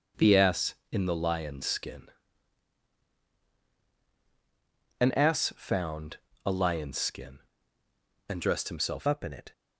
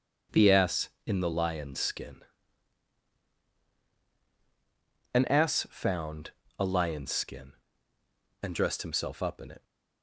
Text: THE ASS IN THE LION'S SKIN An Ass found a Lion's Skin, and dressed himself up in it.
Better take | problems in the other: second | pauses between "SKIN" and "An"; strong; at 2.0 s; 2.9 s long; strong in the second // pauses between "found" and "a"; slight; at 6.1 s; 0.30 s long; slight in the second // changes voice at "up"; from 9.0 s on; 0.5 s long

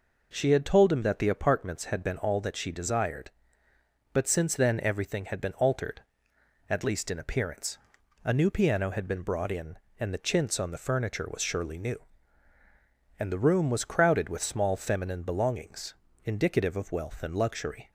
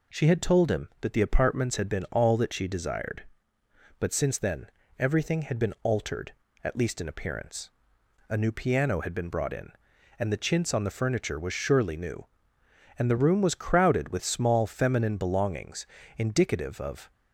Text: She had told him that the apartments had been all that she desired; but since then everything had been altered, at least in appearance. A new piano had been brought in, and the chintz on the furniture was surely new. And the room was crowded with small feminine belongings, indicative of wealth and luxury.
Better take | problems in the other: first | pauses between "then" and "everything"; slight; at 4.6 s; 0.30 s long // stops before "wealth and luxury"; at 17.1 s

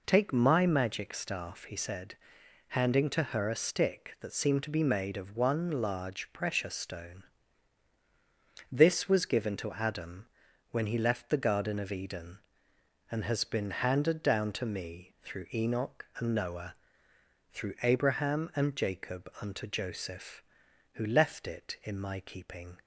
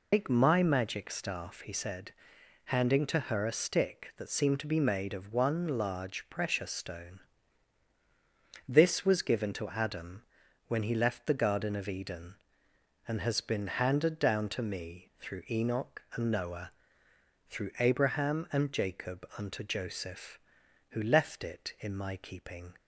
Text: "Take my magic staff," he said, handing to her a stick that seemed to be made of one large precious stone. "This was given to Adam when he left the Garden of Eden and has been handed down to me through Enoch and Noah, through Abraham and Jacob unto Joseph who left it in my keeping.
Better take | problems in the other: first | loses the start of "Take"; at 0.1 s; 100 ms // pauses between "Adam" and "when"; at 10.2 s; 0.44 s long; also in the first

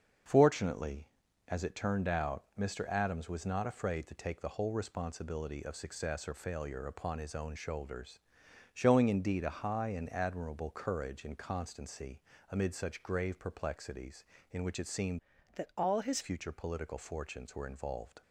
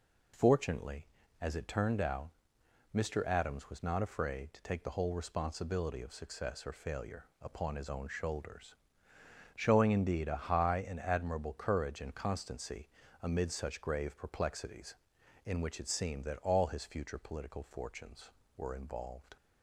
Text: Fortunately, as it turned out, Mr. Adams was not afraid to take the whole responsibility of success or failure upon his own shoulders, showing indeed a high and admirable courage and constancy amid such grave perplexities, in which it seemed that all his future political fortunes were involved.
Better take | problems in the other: second | starts louder than the rest; until 1.6 s; 6.5 dB // pauses between "constancy" and "amid"; slight; at 12.1 s; 0.32 s long; slight in the second // changes voice from "that" to "his"; from 15.5 to 16.2 s; 0.7 s long

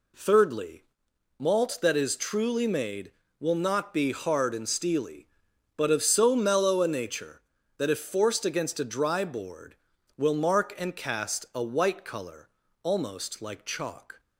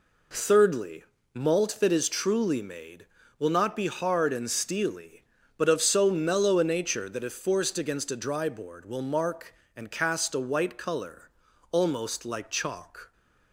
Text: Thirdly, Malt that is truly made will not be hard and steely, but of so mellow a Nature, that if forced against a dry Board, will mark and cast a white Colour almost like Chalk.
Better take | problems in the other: neither | pauses between "Colour" and "almost"; the same in both

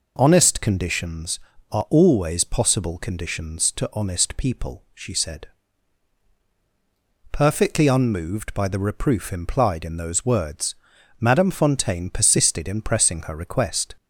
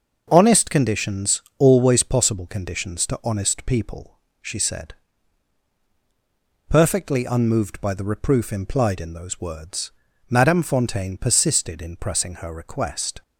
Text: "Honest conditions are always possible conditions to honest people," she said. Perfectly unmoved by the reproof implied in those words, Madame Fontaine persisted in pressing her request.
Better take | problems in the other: first | starts louder than the rest; noticeable; until 1.3 s; 6 dB // skips "are"; at 1.4 s

